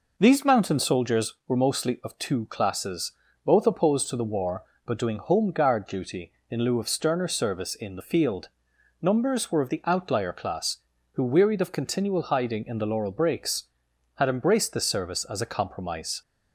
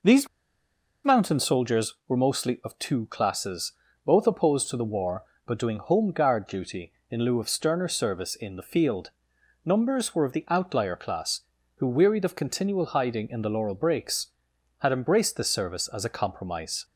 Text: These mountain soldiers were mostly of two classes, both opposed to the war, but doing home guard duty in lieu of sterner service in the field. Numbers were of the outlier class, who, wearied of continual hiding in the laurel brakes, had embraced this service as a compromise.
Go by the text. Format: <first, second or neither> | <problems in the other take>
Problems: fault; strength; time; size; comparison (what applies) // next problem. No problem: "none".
first | pauses between "These" and "mountain"; noticeable; at 0.2 s; 0.78 s long